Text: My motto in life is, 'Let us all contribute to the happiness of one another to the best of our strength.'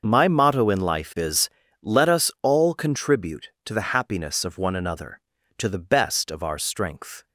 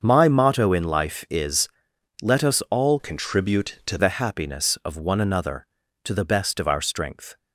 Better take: first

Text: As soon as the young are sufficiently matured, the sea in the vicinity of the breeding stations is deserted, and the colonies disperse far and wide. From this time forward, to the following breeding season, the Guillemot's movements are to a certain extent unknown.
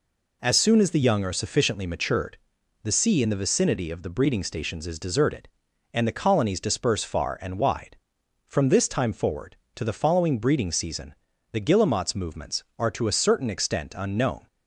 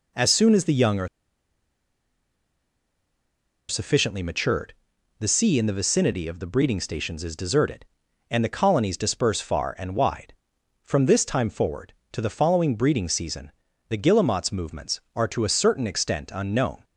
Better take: first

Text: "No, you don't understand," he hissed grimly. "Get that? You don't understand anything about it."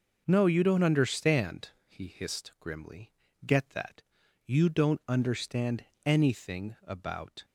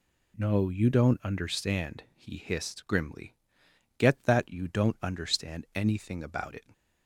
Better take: second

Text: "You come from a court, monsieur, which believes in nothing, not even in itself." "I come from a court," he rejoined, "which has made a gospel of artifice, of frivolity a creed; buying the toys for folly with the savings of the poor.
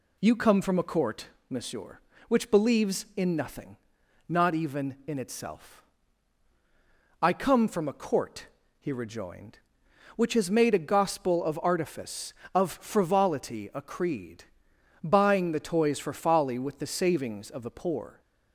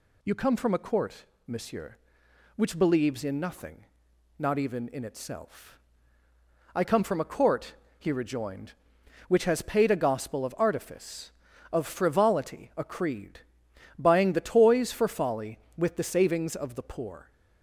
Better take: first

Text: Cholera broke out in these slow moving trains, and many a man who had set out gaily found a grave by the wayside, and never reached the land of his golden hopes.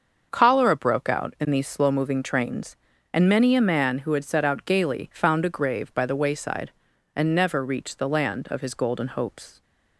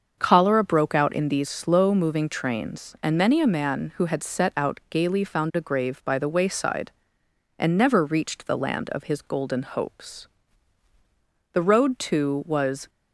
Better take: first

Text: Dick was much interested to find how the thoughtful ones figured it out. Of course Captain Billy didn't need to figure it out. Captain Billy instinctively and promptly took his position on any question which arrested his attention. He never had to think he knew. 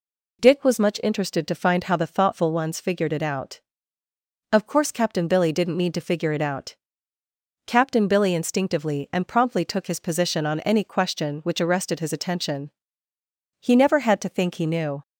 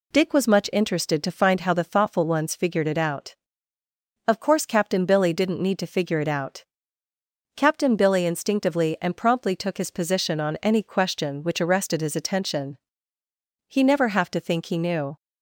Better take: first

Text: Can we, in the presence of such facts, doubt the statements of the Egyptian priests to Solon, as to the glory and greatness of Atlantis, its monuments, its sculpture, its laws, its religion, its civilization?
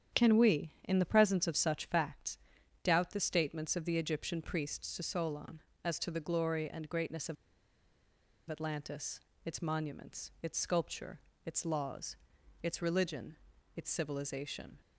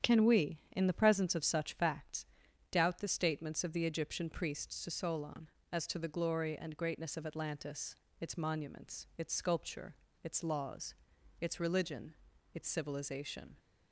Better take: second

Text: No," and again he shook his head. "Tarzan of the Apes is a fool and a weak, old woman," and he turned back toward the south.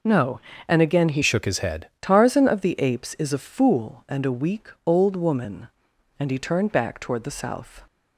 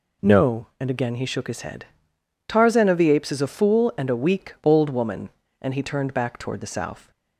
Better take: second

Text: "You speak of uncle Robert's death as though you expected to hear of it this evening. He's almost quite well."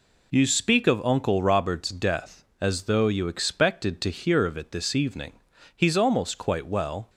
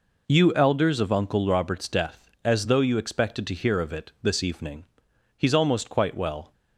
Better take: first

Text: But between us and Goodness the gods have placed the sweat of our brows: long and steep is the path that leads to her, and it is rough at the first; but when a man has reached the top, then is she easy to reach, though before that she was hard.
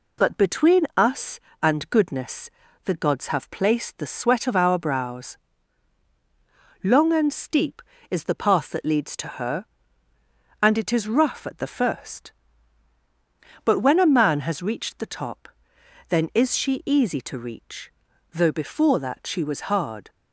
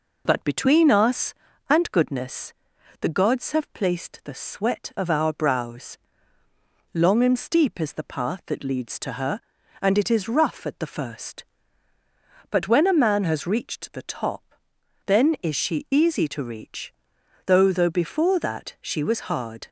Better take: first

